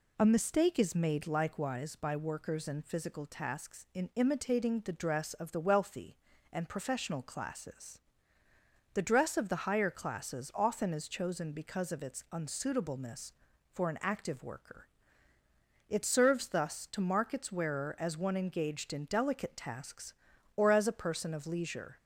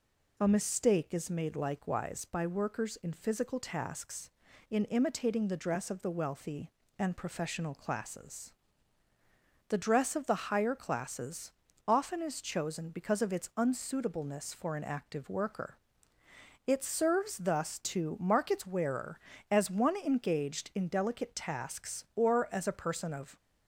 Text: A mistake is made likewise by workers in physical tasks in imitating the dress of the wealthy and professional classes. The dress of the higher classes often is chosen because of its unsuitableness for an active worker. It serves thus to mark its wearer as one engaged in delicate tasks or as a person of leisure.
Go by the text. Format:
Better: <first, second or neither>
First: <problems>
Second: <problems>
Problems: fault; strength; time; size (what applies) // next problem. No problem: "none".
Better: first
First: none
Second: pauses between "classes" and "often"; slight; at 11.5 s; 0.36 s long // stops before "leisure"; at 23.3 s